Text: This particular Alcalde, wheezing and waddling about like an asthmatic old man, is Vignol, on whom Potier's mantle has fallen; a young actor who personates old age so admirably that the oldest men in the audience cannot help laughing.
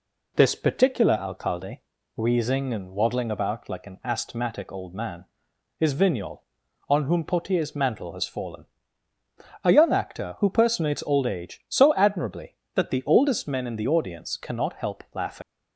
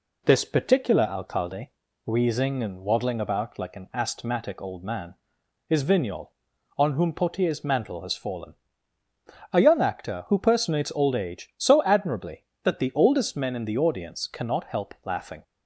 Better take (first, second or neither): second